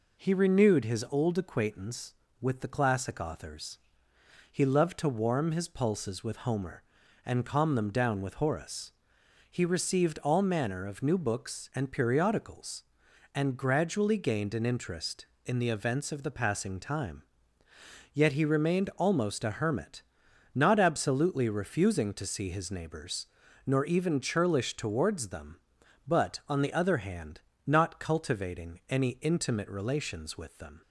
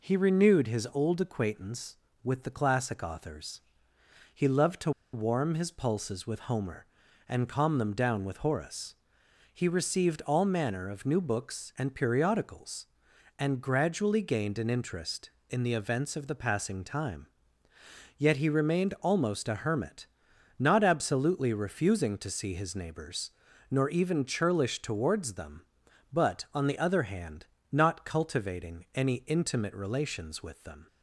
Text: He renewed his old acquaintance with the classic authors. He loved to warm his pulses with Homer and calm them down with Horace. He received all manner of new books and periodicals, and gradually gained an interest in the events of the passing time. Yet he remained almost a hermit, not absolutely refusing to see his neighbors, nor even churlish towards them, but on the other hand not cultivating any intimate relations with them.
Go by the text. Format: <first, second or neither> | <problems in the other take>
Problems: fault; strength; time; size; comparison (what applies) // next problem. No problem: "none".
first | pauses between "to" and "warm"; slight; at 4.9 s; 0.23 s long // pauses between "hand" and "not"; slight; at 27.4 s; 0.26 s long; slight in the first